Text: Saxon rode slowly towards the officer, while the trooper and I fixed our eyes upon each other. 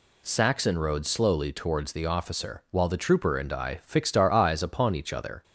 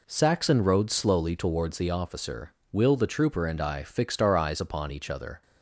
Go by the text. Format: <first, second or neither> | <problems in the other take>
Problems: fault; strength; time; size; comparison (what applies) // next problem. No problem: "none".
first | says "will" for "while"; at 2.7 s